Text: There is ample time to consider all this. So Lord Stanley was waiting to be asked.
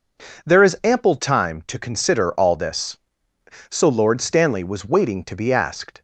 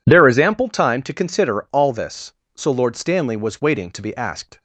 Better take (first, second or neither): neither